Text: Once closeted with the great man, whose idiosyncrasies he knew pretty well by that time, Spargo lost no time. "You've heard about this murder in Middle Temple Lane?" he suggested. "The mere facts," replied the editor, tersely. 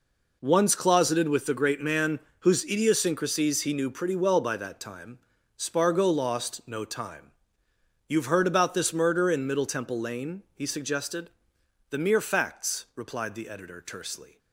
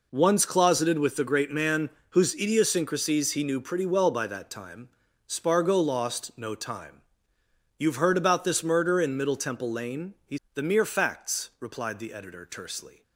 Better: first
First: none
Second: skips "suggested"; at 10.4 s

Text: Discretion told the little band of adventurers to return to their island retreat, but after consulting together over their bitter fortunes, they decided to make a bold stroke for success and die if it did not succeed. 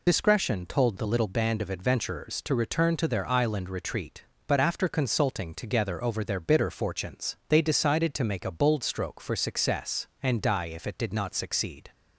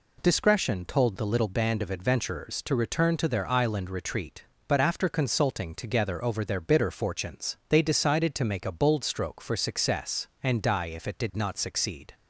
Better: second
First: loses the start of "Discretion"; at 0.0 s; 80 ms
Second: none

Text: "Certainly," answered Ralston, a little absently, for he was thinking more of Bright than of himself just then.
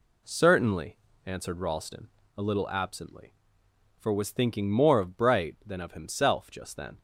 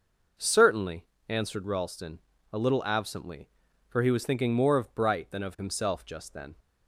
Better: second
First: skips "he"; at 4.1 s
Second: none

